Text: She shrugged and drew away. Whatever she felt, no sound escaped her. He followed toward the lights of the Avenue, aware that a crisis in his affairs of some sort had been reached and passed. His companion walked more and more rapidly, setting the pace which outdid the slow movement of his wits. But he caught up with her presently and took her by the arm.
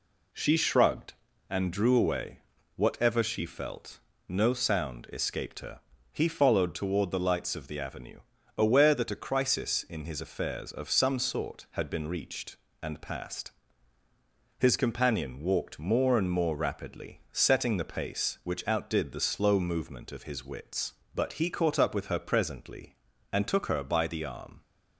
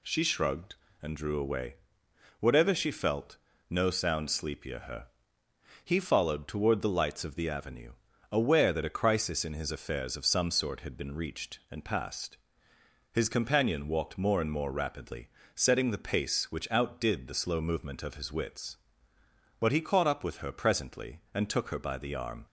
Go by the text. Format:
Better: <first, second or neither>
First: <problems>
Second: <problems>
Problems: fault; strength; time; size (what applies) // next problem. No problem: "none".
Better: first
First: none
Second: says "sleepier" for "escaped"; at 4.2 s